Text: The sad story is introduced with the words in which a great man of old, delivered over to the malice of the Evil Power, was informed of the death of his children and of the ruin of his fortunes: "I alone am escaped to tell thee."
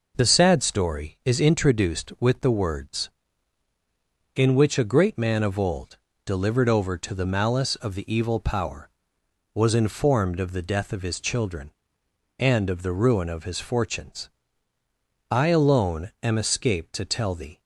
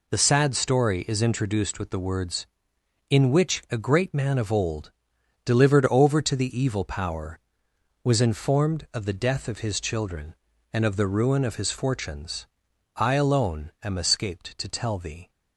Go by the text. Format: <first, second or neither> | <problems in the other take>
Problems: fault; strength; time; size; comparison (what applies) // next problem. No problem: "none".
first | skips "malice of the"; at 6.5 s